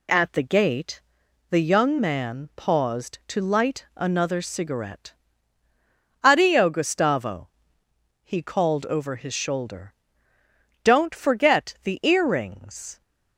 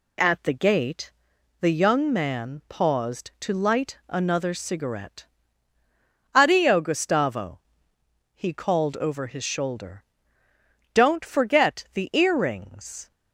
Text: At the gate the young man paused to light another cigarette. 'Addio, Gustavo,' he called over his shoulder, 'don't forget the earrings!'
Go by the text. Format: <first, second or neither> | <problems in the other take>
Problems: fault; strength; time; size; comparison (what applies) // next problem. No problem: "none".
neither | pauses between "gate" and "the"; noticeable; the same in both